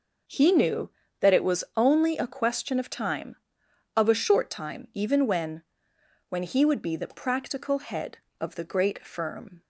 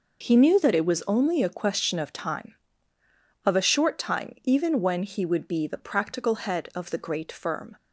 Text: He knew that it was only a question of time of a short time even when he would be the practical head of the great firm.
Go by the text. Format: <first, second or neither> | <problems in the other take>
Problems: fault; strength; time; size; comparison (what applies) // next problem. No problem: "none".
second | says "when" twice; at 6.2 s